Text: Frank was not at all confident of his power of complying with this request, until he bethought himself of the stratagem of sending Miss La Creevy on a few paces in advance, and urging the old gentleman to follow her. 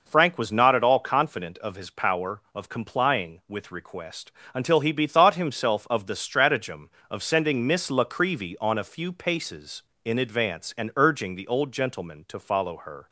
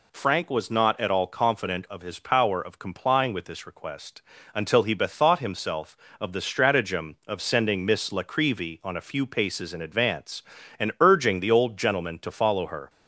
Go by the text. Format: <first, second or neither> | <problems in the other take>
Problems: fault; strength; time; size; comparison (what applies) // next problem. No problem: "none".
second | skips "this"; at 3.7 s